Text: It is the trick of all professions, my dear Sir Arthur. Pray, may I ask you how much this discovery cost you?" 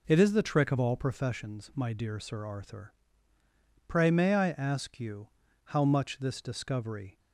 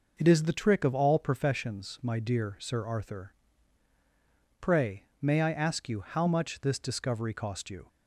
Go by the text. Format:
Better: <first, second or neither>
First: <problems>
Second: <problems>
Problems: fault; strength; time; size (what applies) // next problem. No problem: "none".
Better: second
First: pauses between "you" and "how"; slight; at 5.2 s; 0.36 s long // stops before "cost you"; at 7.1 s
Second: none